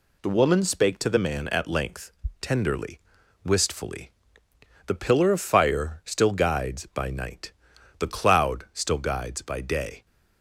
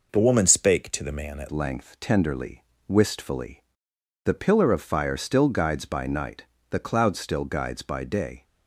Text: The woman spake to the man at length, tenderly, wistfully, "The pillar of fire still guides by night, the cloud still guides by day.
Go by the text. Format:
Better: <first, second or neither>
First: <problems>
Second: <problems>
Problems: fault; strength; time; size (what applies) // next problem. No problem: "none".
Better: first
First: none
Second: changes voice at "length"; from 1.5 s on; 6.9 s long